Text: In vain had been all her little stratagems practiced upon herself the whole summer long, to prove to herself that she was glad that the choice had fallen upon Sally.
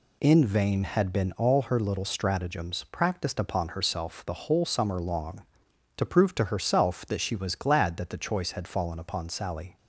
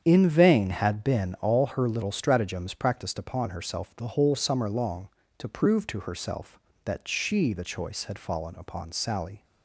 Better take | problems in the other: first | starts louder than the rest; strong; until 1.0 s; 8 dB // skips "was glad that"; at 7.5 s

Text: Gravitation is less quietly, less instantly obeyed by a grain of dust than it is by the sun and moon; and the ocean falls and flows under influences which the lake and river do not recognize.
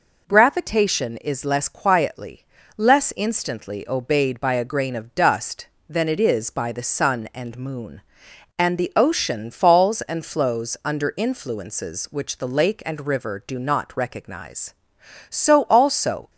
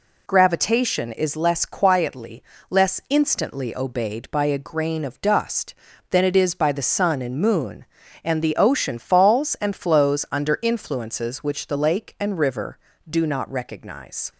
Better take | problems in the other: second | goes on to say "So also"; noticeable; from 15.2 s on; 1.0 s long

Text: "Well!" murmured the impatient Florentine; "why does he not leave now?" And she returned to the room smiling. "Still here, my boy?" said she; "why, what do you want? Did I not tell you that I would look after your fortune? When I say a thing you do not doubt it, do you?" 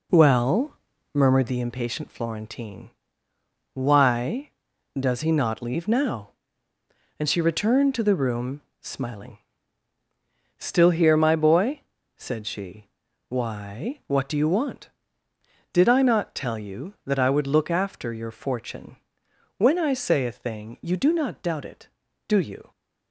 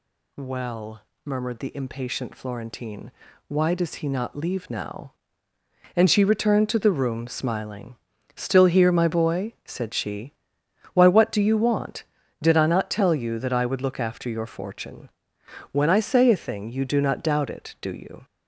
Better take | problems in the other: second | starts louder than the rest; slight; until 1.6 s; 3.5 dB // pauses between "room" and "smiling"; slight; at 8.6 s; 0.20 s long

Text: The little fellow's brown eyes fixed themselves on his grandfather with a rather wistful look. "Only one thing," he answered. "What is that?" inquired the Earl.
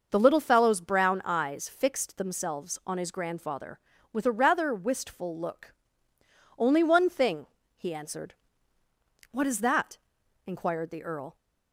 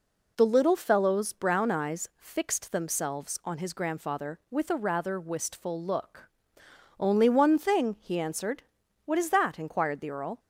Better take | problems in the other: neither | none

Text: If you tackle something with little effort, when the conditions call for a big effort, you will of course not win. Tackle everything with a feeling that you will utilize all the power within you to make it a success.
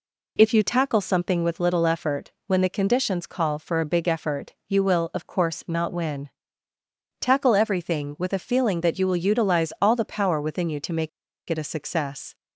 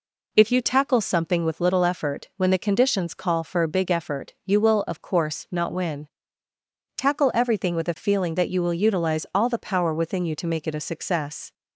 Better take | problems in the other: second | pauses between "make" and "it"; at 11.0 s; 0.38 s long

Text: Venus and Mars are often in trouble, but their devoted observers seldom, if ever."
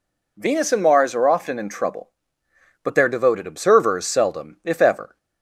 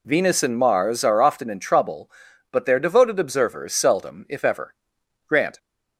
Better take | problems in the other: first | goes on to say "Grant"; slight; from 5.2 s on; 0.32 s long

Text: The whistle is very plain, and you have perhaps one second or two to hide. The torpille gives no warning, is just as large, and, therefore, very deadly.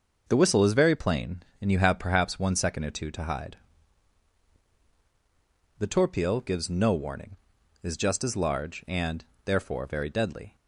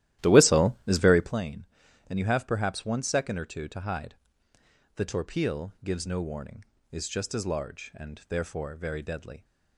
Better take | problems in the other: first | starts louder than the rest; strong; until 1.4 s; 13.5 dB

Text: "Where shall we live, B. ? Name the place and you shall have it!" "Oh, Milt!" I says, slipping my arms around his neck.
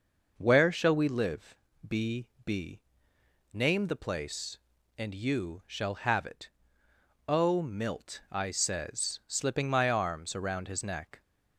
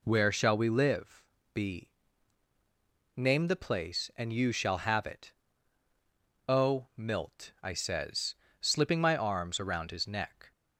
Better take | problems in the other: second | says "B" twice; at 2.4 s

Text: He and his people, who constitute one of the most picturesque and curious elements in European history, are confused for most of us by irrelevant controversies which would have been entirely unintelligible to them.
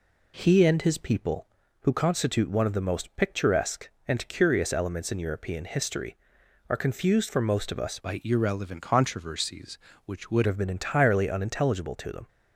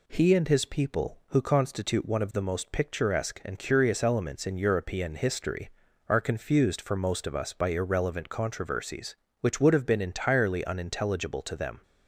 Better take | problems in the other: second | changes voice from "by" to "would"; from 8.0 to 10.4 s; 2.4 s long

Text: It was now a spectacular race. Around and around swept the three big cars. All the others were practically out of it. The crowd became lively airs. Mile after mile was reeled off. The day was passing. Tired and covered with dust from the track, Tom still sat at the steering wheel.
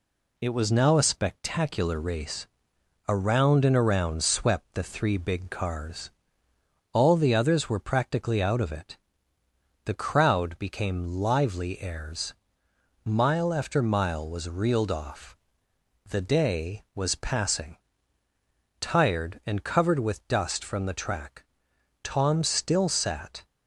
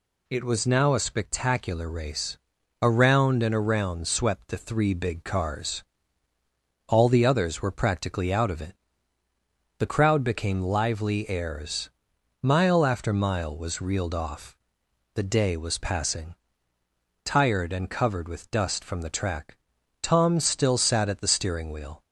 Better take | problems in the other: second | stops before "at the steering wheel"; at 23.4 s

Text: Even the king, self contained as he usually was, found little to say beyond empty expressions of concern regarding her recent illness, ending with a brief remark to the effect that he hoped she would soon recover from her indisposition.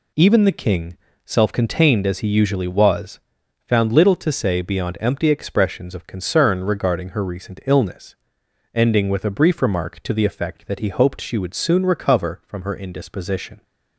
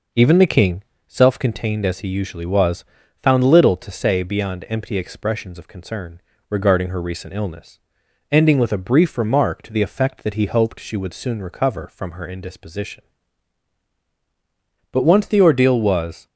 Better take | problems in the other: first | pauses between "concern" and "regarding"; slight; at 6.2 s; 0.28 s long // goes on to say "But once the ordeal was"; from 14.9 s on; 1.3 s long

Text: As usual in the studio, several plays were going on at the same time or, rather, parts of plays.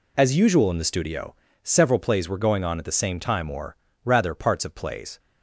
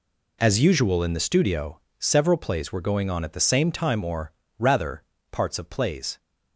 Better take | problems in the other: neither | none

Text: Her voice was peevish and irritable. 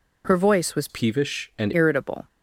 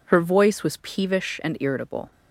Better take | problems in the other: second | changes voice from "peevish" to "and"; from 0.8 to 1.7 s; 0.9 s long

